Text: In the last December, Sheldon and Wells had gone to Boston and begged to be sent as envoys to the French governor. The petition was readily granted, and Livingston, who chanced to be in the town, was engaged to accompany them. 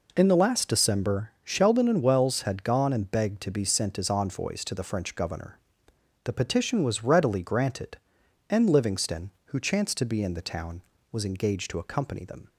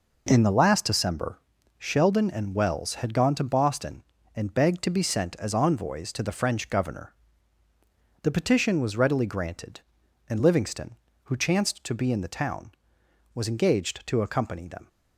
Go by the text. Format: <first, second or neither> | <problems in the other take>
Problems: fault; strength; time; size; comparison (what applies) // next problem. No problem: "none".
second | skips "to Boston"; at 2.9 s